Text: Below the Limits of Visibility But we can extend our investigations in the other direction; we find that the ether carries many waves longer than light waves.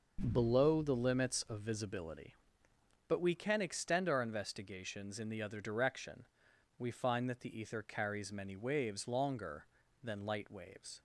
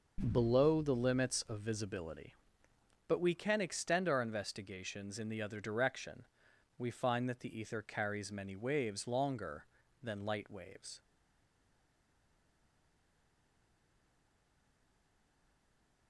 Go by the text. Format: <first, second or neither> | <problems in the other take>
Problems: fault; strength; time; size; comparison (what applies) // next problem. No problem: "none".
first | stays silent after the last word; strong; from 10.9 s on; 5.1 s long